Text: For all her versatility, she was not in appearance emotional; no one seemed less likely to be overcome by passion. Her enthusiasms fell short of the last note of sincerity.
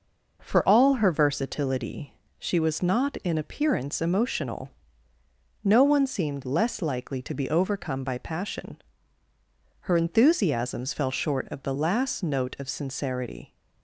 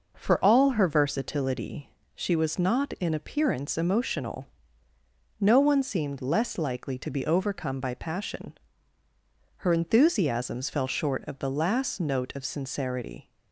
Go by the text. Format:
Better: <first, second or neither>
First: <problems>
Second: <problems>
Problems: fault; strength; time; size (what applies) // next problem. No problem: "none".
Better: neither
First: none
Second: none